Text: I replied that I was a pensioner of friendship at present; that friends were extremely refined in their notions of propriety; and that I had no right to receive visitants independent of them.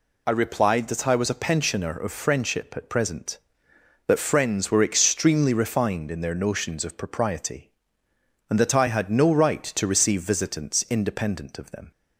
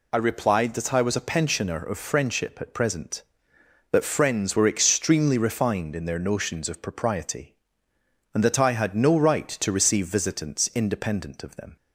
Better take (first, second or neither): neither